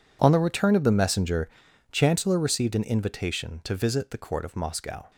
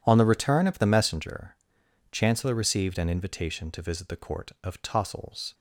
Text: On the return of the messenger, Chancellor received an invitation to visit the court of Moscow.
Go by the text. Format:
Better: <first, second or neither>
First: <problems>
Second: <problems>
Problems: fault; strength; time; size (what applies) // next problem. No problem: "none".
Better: first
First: none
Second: says "Tossels" for "Moscow"; at 4.8 s